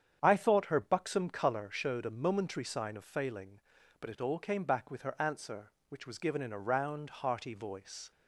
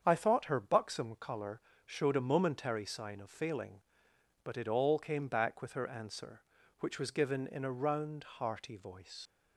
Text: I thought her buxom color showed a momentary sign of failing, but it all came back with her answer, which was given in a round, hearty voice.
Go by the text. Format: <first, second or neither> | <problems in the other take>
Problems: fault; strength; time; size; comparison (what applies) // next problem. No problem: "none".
first | starts louder than the rest; strong; until 1.0 s; 7.5 dB; strong in the first // pauses between "color" and "showed"; slight; at 1.6 s; 0.24 s long // leaves "voice" unfinished; at 9.2 s; 75 ms